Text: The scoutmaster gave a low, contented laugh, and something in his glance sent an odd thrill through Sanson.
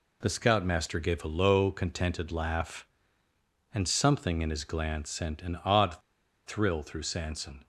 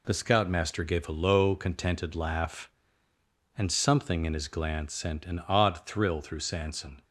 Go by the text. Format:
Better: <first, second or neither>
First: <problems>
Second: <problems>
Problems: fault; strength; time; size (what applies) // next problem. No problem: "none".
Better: second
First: pauses between "odd" and "thrill"; noticeable; at 5.9 s; 0.48 s long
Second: none